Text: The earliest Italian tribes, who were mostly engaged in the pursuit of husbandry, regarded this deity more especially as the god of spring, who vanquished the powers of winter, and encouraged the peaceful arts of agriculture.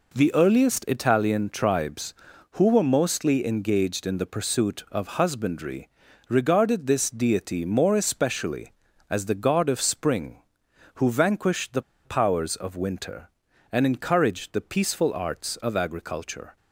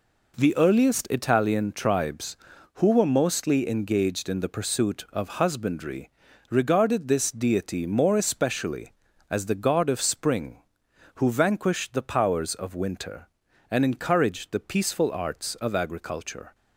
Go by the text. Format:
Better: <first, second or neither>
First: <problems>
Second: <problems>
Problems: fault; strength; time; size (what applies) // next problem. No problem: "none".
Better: second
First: pauses between "the" and "powers"; slight; at 11.8 s; 0.24 s long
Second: none